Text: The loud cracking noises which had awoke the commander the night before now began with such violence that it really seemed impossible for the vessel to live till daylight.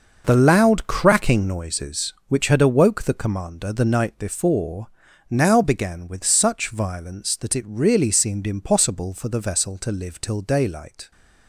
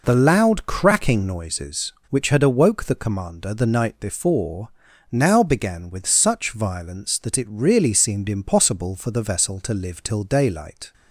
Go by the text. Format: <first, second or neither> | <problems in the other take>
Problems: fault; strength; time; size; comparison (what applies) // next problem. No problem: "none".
second | gets quieter; strong; throughout; 10.5 dB // pauses between "before" and "now"; at 4.8 s; 0.42 s long; also in the second